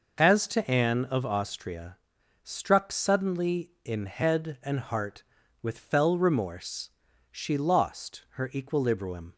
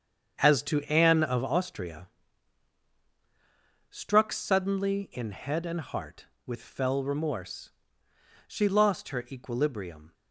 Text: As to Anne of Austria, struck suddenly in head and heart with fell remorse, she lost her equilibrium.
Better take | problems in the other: first | gets quieter; strong; throughout; 9.5 dB

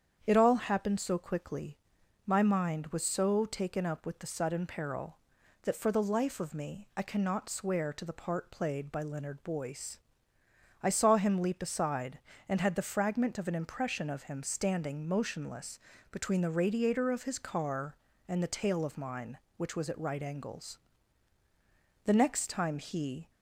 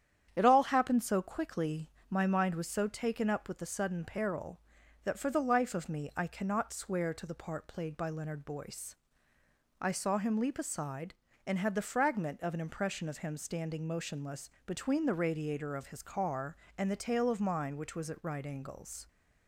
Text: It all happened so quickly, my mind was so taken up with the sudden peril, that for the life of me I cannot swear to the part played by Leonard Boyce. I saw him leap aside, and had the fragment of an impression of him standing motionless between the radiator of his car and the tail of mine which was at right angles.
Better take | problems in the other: second | starts louder than the rest; strong; until 1.2 s; 8 dB; strong in the second // pauses between "motionless" and "between"; slight; at 15.7 s; 0.32 s long; slight in the second // goes on to say "The next time he"; noticeable; from 22.0 s on; 1.2 s long

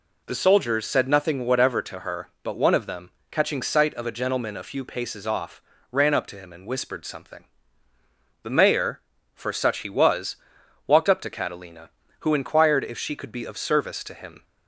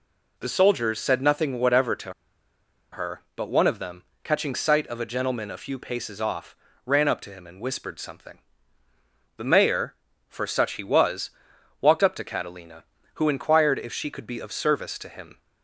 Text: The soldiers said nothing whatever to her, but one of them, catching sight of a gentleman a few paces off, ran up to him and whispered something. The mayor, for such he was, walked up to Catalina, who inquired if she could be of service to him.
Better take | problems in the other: first | pauses between "to" and "her"; noticeable; at 2.1 s; 0.79 s long

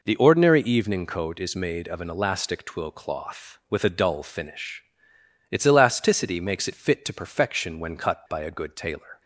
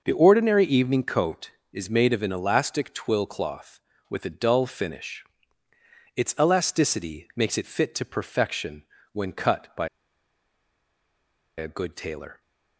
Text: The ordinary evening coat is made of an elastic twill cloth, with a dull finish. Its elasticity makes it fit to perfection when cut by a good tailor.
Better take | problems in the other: first | pauses between "perfection" and "when"; slight; at 8.8 s; 0.30 s long // pauses between "by" and "a"; strong; at 9.8 s; 1.6 s long

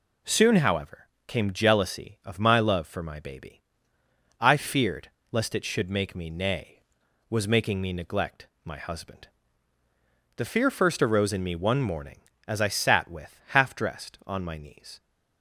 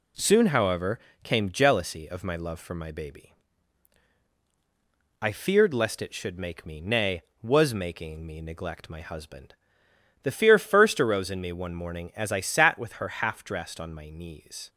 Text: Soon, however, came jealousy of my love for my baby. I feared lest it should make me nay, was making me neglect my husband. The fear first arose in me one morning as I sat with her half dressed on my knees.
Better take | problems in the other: second | pauses between "feared" and "lest"; slight; at 5.0 s; 0.22 s long // pauses between "neglect" and "my"; slight; at 8.4 s; 0.16 s long // skips "her"; at 13.4 s

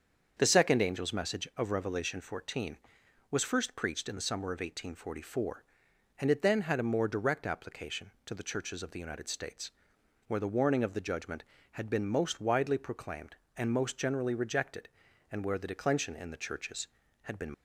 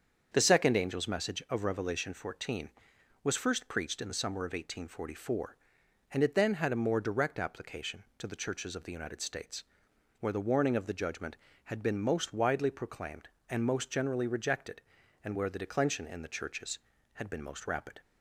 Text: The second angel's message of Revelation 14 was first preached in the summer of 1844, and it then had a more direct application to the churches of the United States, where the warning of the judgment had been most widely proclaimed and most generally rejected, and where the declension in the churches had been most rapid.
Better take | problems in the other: second | starts louder than the rest; strong; until 1.3 s; 7 dB; strong in the second // stops before "most rapid"; at 17.5 s

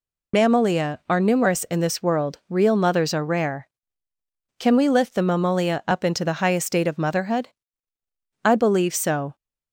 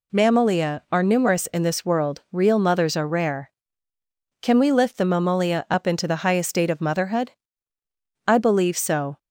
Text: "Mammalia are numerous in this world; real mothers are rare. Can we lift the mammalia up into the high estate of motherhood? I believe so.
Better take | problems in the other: second | loses the start of "Mammalia"; at 0.3 s; 45 ms

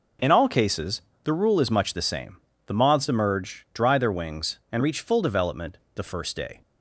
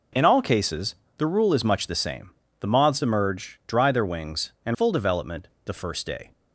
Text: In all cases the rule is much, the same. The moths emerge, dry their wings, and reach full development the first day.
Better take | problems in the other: first | pauses between "cases" and "the"; slight; at 0.9 s; 0.24 s long; slight in the first // skips "reach"; at 4.7 s // pauses between "development" and "the"; slight; at 5.4 s; 0.18 s long; slight in the first

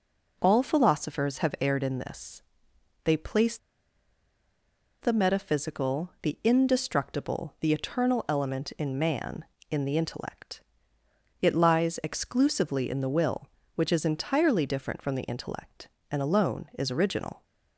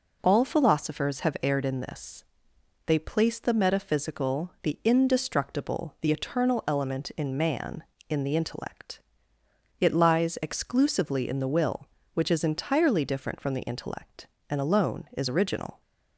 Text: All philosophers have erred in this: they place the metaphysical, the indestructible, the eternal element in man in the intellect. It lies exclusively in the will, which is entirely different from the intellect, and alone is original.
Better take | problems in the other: second | pauses between "place" and "the"; strong; at 3.5 s; 1.4 s long

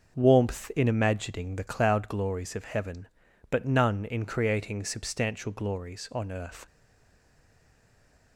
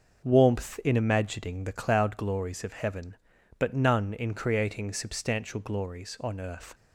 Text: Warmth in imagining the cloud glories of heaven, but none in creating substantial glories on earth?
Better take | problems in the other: second | starts louder than the rest; until 1.1 s; 6.5 dB; also in the second // stays silent after the last word; noticeable; from 6.6 s on; 1.7 s long

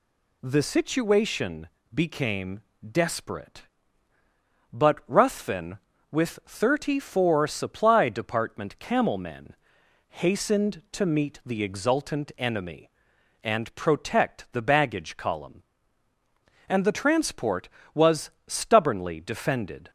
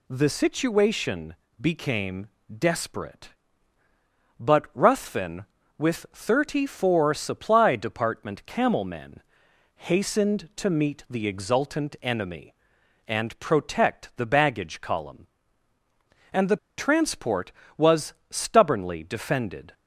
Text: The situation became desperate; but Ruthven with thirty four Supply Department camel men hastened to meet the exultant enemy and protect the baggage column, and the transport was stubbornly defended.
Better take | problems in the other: first | pauses between "situation" and "became"; slight; at 1.3 s; 0.24 s long; slight in the first // pauses between "became" and "desperate"; slight; at 2.2 s; 0.32 s long; slight in the first // pauses between "men" and "hastened"; noticeable; at 9.2 s; 0.56 s long; noticeable in the first // pauses between "the" and "transport"; slight; at 16.5 s; 0.20 s long // pauses between "was" and "stubbornly"; slight; at 18.1 s; 0.16 s long; slight in the first

